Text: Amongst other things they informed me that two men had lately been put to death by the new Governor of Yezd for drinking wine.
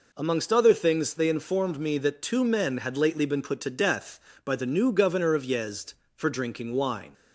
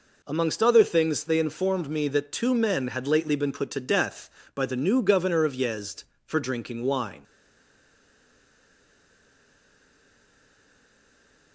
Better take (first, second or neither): first